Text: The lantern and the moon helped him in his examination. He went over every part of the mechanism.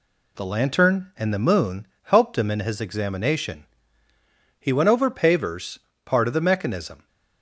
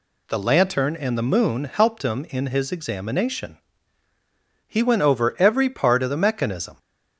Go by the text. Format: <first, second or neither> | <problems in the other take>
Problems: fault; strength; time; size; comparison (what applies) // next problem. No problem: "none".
second | pauses between "moon" and "helped"; slight; at 1.8 s; 0.18 s long // says "pavers" for "every"; at 5.1 s